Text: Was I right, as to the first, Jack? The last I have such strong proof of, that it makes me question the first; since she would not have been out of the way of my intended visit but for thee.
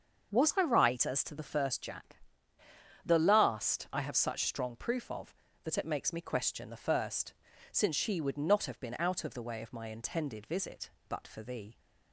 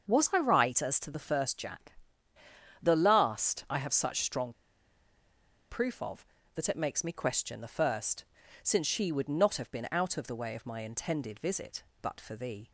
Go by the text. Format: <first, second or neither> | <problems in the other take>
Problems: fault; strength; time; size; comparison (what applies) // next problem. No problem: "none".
first | starts louder than the rest; until 1.1 s; 6.5 dB; also in the first // pauses between "strong" and "proof"; at 4.5 s; 1.1 s long